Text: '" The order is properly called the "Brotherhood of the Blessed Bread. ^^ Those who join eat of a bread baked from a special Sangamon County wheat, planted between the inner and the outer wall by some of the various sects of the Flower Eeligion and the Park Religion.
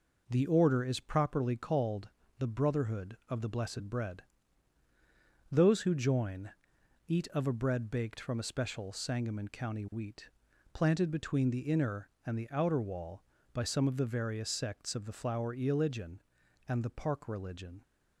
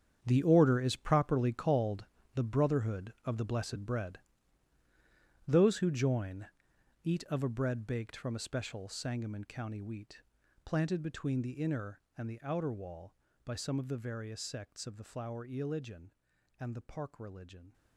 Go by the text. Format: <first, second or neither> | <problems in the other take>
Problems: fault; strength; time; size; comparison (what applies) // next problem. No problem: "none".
first | gets quieter; strong; throughout; 13.5 dB // pauses between "called" and "the"; slight; at 2.0 s; 0.32 s long; slight in the first // pauses between "join" and "eat"; noticeable; at 6.4 s; 0.56 s long; noticeable in the first